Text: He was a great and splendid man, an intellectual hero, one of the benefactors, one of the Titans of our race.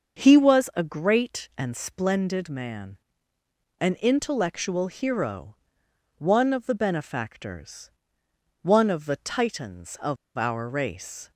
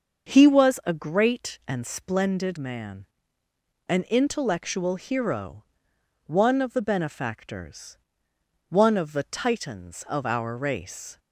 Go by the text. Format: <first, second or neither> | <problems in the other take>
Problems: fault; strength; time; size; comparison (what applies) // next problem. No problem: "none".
second | starts louder than the rest; until 1.2 s; 6 dB; also in the second // pauses between "of" and "our"; slight; at 10.1 s; 0.20 s long